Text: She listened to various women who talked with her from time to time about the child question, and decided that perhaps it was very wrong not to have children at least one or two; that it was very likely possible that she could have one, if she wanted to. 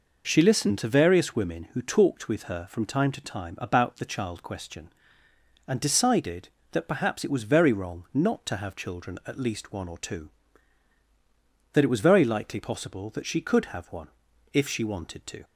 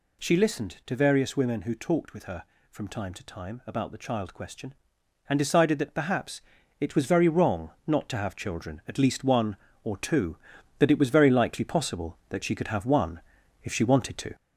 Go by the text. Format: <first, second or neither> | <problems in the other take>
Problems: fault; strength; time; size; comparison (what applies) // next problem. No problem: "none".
first | gets louder; slight; throughout; 3.5 dB // pauses between "perhaps" and "it"; at 6.4 s; 0.38 s long // pauses between "wrong" and "not"; slight; at 7.7 s; 0.16 s long